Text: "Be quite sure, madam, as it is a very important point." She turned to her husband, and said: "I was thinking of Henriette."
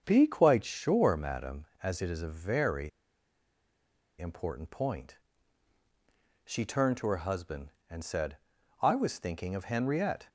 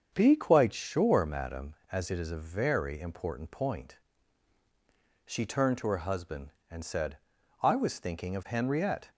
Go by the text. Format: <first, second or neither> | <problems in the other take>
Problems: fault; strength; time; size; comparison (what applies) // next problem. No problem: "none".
second | starts louder than the rest; strong; until 1.0 s; 7 dB; strong in the second // pauses between "very" and "important"; strong; at 2.8 s; 1.3 s long